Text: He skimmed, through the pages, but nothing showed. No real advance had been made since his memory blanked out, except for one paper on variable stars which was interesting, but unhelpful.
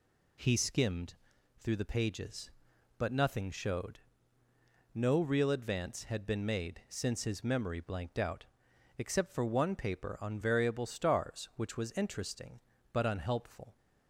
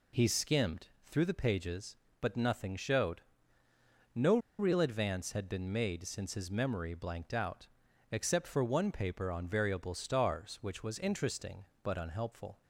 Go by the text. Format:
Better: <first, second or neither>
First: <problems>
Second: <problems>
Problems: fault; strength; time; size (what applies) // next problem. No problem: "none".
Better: first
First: none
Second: pauses between "No" and "real"; slight; at 4.3 s; 0.20 s long